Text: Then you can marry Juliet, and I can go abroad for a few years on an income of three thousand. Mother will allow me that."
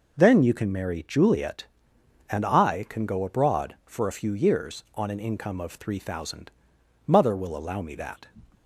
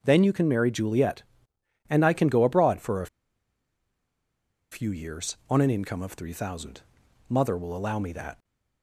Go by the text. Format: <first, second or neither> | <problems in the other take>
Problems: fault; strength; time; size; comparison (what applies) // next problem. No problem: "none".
first | pauses between "a" and "few"; strong; at 3.0 s; 1.6 s long